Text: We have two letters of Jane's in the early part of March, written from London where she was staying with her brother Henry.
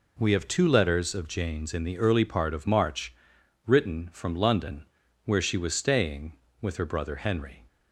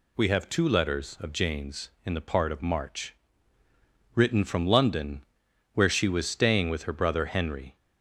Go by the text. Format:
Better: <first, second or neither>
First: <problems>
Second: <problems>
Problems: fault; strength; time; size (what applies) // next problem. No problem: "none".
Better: first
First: pauses between "London" and "where"; at 4.8 s; 0.40 s long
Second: skips "early"; at 2.2 s // pauses between "London" and "where"; noticeable; at 5.2 s; 0.48 s long